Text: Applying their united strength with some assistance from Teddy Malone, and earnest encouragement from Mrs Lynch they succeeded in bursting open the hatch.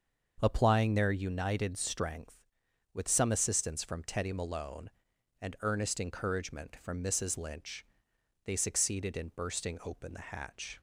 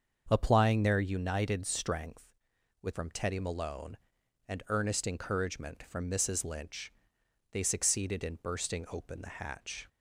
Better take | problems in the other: first | starts louder than the rest; until 1.3 s; 7 dB; also in the first // skips "some assistance"; at 2.9 s // pauses between "Lynch" and "they"; noticeable; at 6.9 s; 0.60 s long; noticeable in the first

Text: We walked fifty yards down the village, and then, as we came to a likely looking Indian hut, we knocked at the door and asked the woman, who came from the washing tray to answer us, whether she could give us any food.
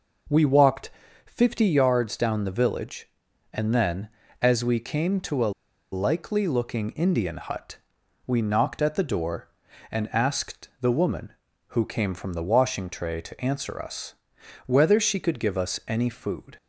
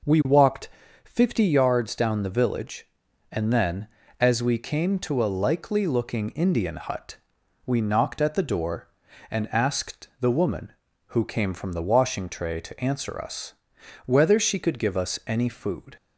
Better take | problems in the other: second | pauses between "walked" and "fifty"; slight; at 0.8 s; 0.36 s long; slight in the second // pauses between "a" and "likely"; at 5.5 s; 0.39 s long

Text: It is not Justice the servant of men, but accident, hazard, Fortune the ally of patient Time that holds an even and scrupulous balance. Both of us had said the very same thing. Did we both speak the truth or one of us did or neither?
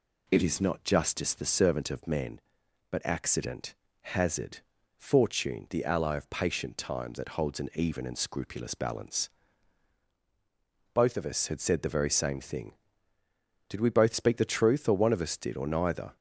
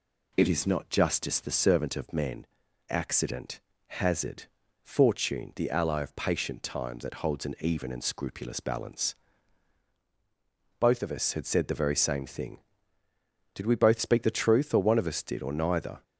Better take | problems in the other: first | skips "but"; at 2.6 s

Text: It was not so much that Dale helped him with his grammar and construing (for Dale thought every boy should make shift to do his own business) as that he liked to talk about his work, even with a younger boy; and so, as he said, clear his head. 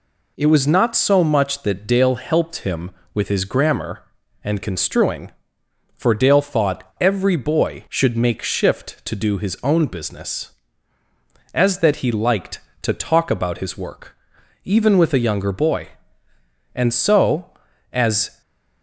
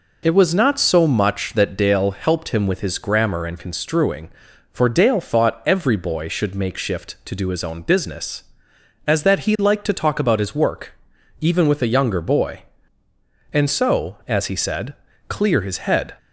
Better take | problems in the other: second | stops before "he said clear his head"; at 18.4 s

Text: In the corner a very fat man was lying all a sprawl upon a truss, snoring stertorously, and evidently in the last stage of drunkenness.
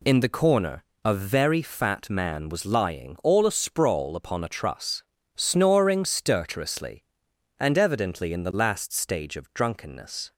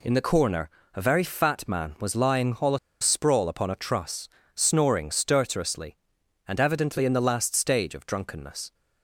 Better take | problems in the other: first | pauses between "corner" and "a"; slight; at 0.6 s; 0.24 s long; slight in the first // pauses between "a" and "sprawl"; slight; at 2.7 s; 0.23 s long

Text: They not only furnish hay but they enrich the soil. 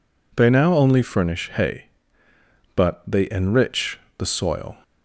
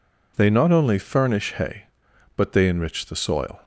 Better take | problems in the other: second | says "now" for "not"; at 0.4 s // pauses between "enrich" and "the"; slight; at 3.9 s; 0.18 s long

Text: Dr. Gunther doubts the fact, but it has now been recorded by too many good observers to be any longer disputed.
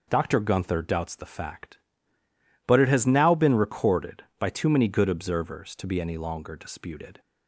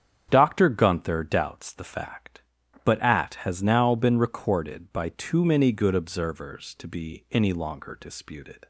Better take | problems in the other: first | starts louder than the rest; strong; until 1.3 s; 9 dB // says "at" for "it"; at 3.0 s

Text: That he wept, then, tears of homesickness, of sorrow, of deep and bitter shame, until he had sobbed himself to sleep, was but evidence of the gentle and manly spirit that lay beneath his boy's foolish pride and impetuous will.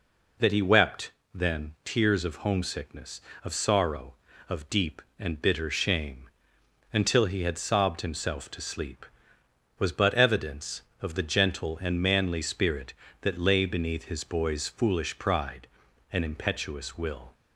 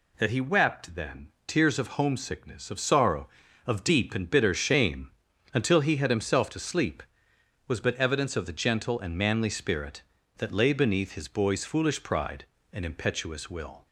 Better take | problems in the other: first | skips "sobbed"; at 6.0 s

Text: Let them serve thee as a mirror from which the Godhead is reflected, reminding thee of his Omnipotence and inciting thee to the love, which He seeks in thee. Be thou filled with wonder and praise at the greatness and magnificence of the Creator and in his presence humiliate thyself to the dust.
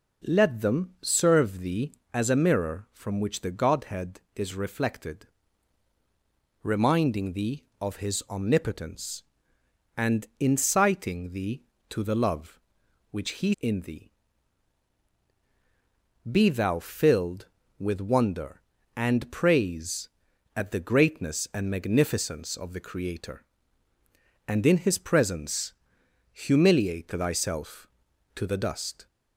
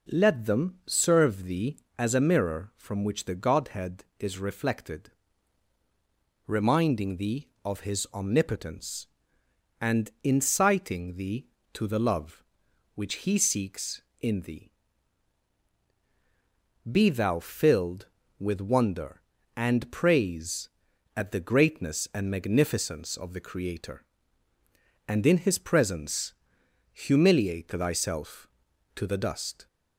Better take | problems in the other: second | skips "seeks"; at 13.5 s // pauses between "presence" and "humiliate"; noticeable; at 25.7 s; 0.60 s long; noticeable in the second

